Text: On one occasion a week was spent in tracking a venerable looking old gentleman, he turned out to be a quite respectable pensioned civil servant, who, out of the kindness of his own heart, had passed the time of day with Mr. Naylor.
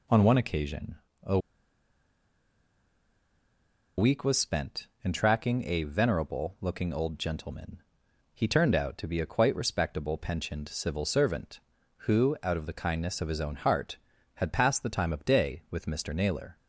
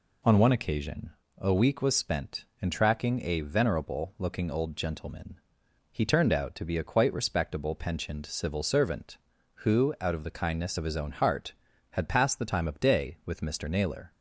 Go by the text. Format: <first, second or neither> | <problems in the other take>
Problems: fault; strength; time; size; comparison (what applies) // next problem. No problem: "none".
second | pauses between "occasion" and "a"; slight; at 0.9 s; 0.24 s long; slight in the second // pauses between "a" and "week"; strong; at 1.3 s; 2.5 s long